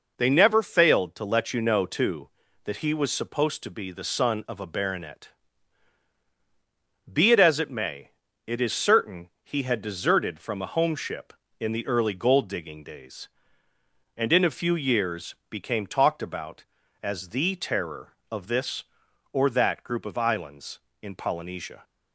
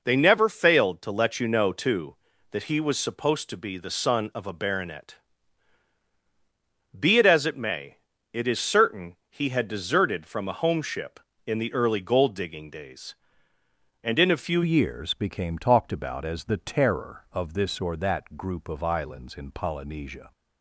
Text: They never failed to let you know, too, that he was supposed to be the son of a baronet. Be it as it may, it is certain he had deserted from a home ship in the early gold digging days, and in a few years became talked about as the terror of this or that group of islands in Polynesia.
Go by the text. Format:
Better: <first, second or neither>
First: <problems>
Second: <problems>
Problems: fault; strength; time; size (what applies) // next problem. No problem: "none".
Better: first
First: none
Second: changes voice at "years"; from 14.6 s on; 5.7 s long